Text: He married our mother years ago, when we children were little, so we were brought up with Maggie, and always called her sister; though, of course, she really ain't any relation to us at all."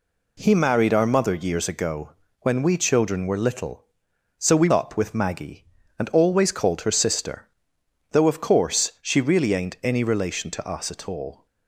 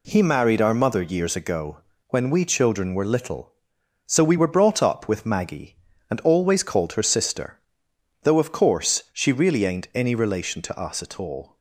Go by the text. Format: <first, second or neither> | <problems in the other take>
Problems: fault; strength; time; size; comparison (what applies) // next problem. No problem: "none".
second | skips "were brought"; at 4.6 s